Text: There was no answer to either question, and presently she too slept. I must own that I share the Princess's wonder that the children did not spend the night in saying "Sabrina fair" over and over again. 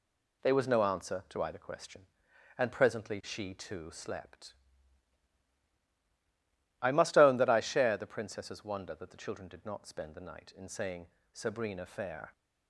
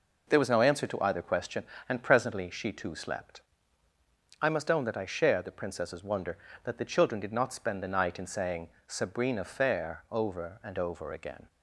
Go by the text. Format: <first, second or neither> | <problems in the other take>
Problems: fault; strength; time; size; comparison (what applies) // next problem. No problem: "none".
second | pauses between "saying" and "Sabrina"; slight; at 11.0 s; 0.26 s long; slight in the second // stops before "over and over again"; at 12.3 s